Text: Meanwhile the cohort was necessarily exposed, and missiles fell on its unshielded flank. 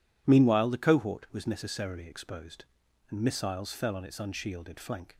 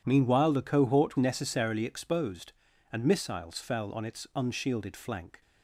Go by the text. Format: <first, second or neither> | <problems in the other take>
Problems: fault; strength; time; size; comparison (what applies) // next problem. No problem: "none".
first | skips "was"; at 1.1 s